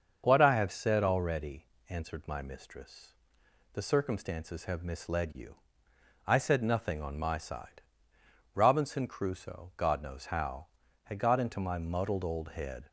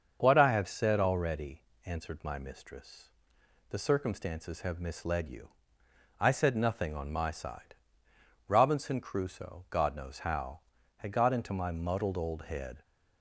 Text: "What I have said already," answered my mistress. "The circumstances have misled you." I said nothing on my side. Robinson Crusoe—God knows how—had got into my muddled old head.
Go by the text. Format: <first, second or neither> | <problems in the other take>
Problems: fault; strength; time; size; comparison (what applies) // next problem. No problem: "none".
neither | starts louder than the rest; the same in both